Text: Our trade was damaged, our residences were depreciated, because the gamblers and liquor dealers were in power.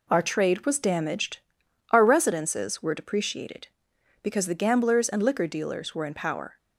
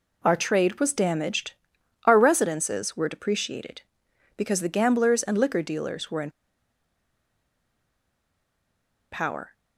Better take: first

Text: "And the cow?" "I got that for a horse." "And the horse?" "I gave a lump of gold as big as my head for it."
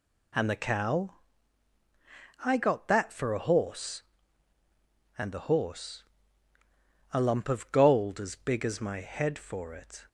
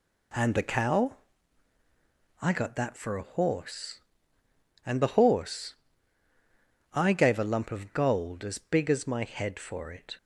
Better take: second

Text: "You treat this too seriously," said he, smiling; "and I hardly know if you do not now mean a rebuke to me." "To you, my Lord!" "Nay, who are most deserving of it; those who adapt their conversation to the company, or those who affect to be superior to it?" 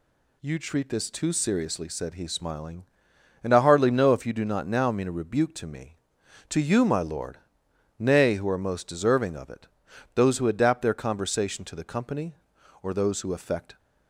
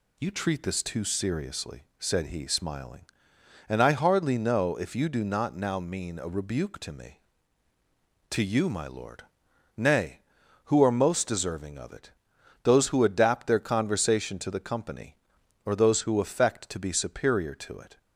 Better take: second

